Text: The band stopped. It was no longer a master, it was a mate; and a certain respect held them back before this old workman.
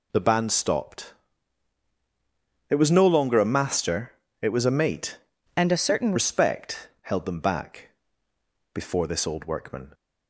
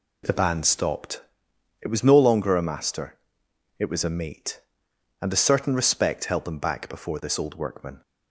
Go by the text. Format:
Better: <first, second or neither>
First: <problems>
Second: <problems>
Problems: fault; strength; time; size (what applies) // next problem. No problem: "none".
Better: second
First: changes voice from "and" to "certain"; from 5.5 to 6.1 s; 0.6 s long // pauses between "back" and "before"; noticeable; at 7.8 s; 0.82 s long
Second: none